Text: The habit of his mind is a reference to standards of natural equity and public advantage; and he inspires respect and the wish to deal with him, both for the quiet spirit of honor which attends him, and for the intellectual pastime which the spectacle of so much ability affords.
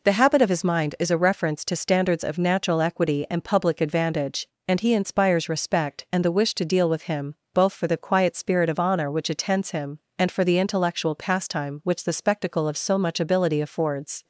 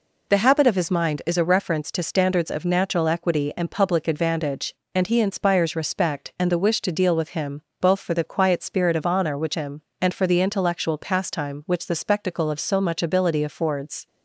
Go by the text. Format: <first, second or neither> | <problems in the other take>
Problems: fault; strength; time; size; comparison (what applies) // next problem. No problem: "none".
first | skips "attends"; at 9.5 s